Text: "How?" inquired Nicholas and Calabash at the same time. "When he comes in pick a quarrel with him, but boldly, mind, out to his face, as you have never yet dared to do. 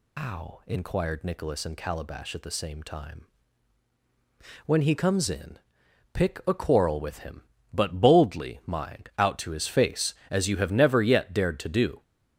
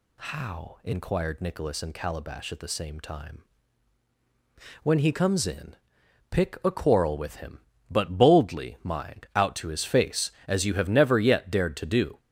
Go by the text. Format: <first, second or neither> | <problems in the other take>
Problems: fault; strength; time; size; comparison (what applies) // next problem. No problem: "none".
second | loses the start of "How"; at 0.1 s; 145 ms // pauses between "in" and "pick"; noticeable; at 5.5 s; 0.52 s long; noticeable in the second